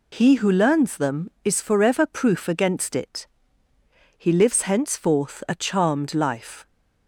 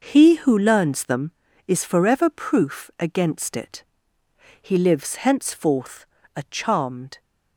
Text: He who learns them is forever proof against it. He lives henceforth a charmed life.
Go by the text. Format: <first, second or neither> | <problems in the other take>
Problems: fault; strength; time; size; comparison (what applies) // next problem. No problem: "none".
first | pauses between "henceforth" and "a"; slight; at 6.0 s; 0.30 s long // stops before "life"; at 7.1 s